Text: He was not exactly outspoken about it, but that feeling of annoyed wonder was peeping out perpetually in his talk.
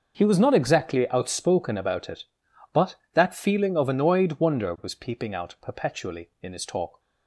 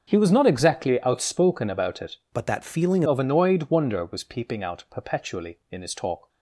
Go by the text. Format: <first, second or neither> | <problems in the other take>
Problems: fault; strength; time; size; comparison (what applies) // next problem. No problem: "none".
first | starts louder than the rest; until 1.1 s; 6.5 dB; also in the first // changes voice from "but" to "feeling"; from 2.3 to 3.0 s; 0.7 s long